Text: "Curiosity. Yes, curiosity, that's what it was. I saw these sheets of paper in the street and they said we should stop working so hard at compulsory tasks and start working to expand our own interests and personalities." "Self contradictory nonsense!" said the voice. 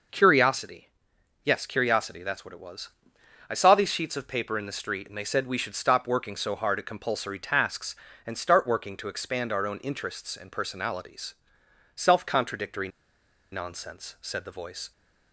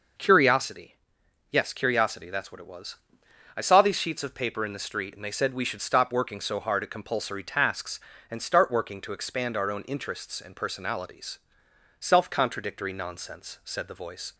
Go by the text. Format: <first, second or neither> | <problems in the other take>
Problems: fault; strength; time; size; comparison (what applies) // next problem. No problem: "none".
second | pauses between "contradictory" and "nonsense"; noticeable; at 12.8 s; 0.63 s long